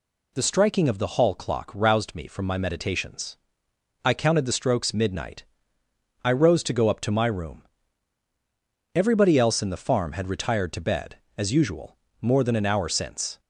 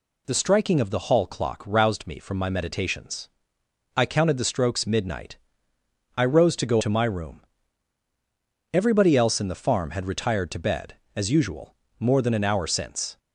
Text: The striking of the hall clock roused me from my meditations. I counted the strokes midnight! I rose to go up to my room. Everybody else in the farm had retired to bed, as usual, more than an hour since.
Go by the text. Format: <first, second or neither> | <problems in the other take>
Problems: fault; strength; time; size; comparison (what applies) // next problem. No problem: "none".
first | skips "up"; at 6.8 s